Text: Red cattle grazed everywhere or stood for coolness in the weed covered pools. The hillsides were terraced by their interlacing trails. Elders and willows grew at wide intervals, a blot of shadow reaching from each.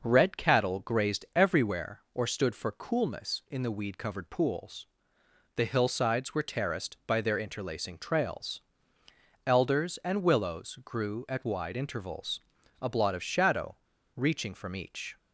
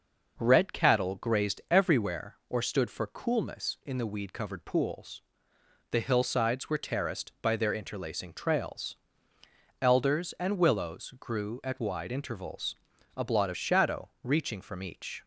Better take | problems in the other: second | pauses between "shadow" and "reaching"; at 13.7 s; 0.40 s long

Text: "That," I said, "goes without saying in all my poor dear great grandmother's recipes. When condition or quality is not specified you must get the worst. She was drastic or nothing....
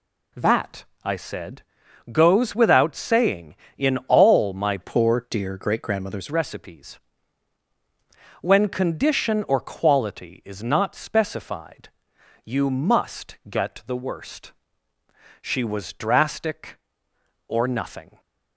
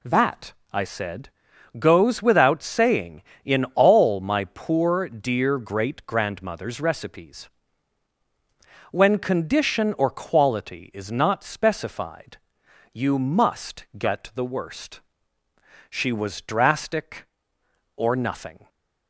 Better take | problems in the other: second | changes voice from "poor" to "grandmother's"; from 4.8 to 6.2 s; 1.4 s long // pauses between "specified" and "you"; noticeable; at 11.8 s; 0.56 s long; noticeable in the second

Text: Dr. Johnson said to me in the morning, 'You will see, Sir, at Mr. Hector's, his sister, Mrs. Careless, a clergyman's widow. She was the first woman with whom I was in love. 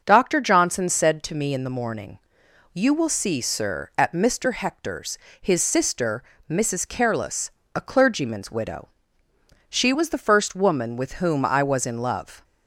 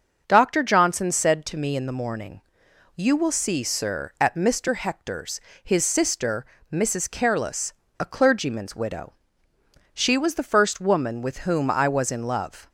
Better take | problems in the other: neither | starts louder than the rest; the same in both

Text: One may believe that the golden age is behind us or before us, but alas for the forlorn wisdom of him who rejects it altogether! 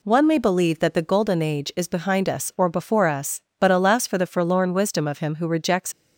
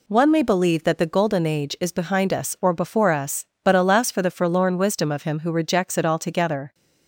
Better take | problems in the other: second | stops before "it altogether"; at 5.9 s

